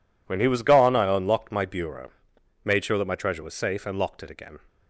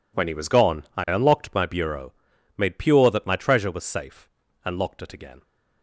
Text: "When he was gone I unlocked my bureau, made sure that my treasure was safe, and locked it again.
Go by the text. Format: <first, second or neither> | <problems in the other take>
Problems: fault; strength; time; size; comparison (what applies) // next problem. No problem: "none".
first | says "pure" for "sure"; at 2.7 s